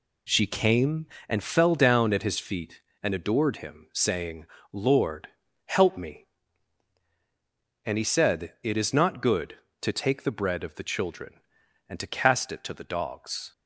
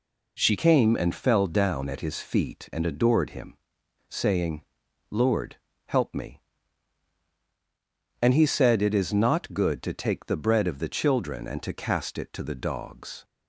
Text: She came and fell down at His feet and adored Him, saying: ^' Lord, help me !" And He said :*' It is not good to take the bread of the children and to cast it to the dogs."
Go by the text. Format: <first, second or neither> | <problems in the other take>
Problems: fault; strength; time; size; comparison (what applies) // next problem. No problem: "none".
first | changes voice at "came"; from 0.5 s on; 12.7 s long